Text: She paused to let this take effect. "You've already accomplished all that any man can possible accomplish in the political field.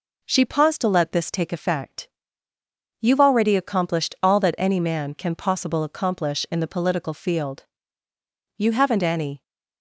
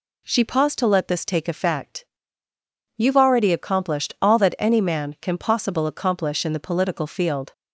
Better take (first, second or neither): second